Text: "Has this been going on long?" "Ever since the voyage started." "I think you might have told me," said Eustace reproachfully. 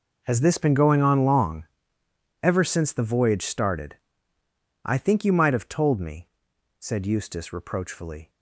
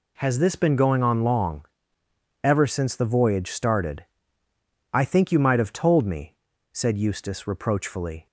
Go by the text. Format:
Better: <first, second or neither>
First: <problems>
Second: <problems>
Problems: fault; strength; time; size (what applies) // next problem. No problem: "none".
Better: second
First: gets quieter; strong; throughout; 15 dB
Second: none